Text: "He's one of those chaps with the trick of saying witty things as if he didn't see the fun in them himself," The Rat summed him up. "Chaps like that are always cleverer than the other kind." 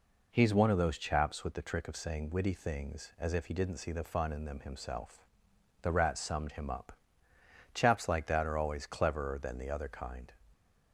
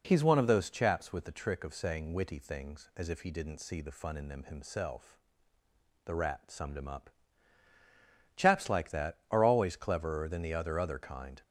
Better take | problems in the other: first | says "other" twice; at 10.7 s

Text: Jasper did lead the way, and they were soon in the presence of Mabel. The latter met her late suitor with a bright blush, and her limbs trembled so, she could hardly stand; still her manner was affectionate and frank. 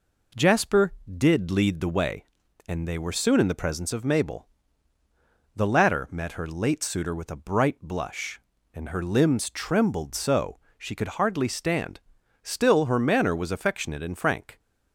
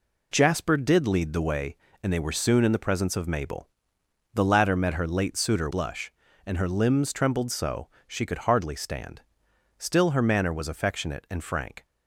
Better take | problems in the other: first | skips "with a bright"; at 5.7 s

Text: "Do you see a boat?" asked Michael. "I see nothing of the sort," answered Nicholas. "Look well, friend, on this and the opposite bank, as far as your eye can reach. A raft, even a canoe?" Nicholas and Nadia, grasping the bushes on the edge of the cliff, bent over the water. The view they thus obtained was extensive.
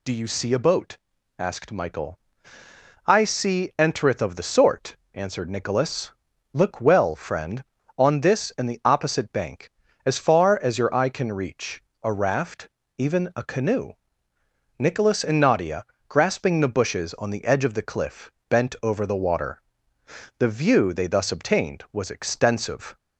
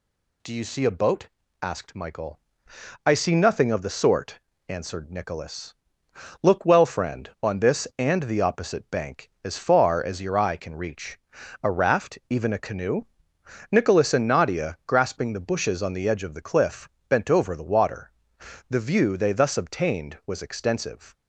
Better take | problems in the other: second | says "entereth" for "nothing"; at 3.7 s

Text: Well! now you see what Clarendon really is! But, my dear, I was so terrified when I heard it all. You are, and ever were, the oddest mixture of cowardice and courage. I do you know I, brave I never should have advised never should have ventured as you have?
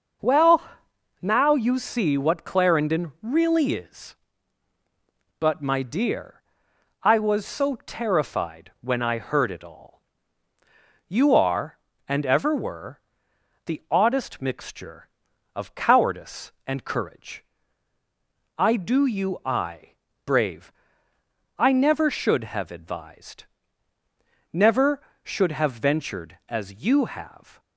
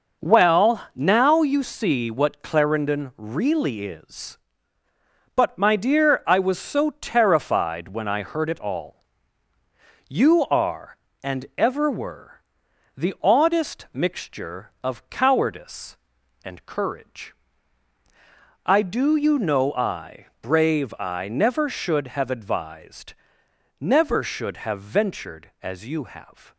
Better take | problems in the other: second | starts louder than the rest; noticeable; until 1.8 s; 6 dB // skips "know"; at 19.4 s // pauses between "brave" and "I"; noticeable; at 20.7 s; 0.86 s long // pauses between "advised" and "never"; at 23.4 s; 1.0 s long; noticeable in the second

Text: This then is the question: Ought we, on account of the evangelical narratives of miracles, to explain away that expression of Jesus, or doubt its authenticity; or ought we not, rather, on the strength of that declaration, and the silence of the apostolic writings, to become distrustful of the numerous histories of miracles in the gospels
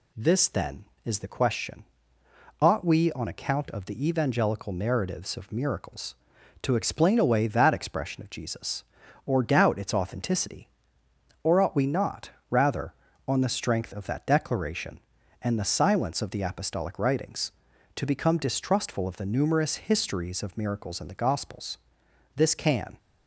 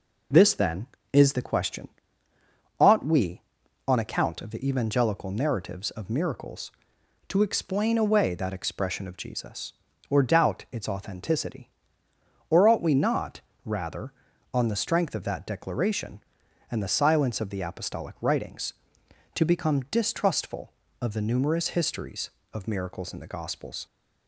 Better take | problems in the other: second | goes on to say "This can"; noticeable; from 22.3 s on; 0.62 s long

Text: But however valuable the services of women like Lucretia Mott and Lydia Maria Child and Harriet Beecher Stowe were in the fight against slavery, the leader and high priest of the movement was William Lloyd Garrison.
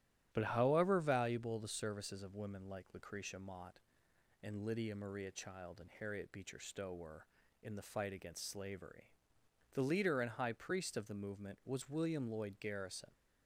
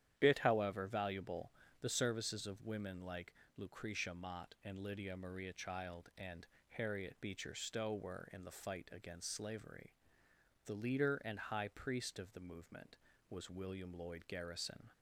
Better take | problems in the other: first | starts louder than the rest; strong; until 1.1 s; 10.5 dB; strong in the first // says "Bit" for "But"; at 0.1 s // pauses between "valuable" and "the"; slight; at 1.5 s; 0.30 s long // pauses between "like" and "Lucretia"; slight; at 3.3 s; 0.24 s long // pauses between "and" and "Harriet"; slight; at 6.4 s; 0.24 s long

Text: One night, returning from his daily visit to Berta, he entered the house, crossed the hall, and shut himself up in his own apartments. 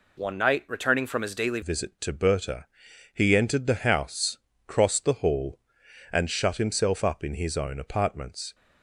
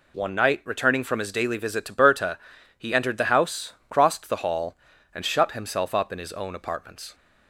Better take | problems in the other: second | changes voice at "visit"; from 1.6 s on; 6.9 s long

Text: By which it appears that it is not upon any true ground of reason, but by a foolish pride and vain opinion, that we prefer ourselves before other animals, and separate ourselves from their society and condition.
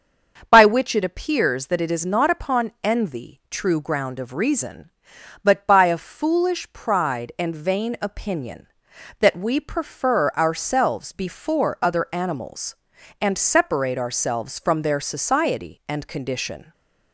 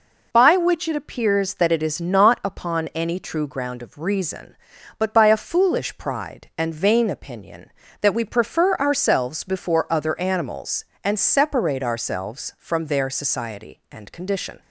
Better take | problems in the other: second | starts louder than the rest; until 1.5 s; 7 dB // says "envy" for "any"; at 2.8 s // stays silent after the last word; slight; from 16.6 s on; 0.5 s long

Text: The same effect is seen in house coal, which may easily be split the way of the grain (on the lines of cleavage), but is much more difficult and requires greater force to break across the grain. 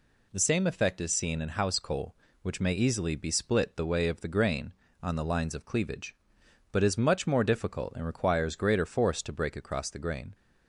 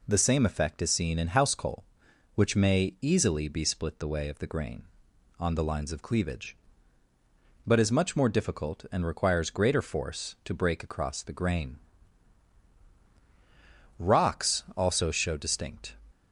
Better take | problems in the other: first | goes on to say "Rocks also show distinct"; strong; from 14.0 s on; 1.9 s long

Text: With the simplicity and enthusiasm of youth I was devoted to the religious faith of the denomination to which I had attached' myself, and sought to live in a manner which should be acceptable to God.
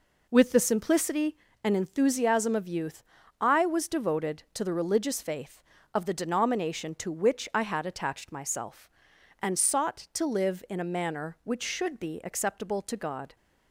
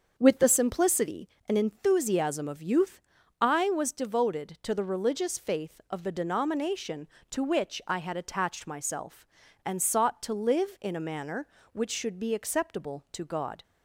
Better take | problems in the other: first | starts louder than the rest; until 1.2 s; 6.5 dB // pauses between "youth" and "I"; at 3.0 s; 0.40 s long; also in the first

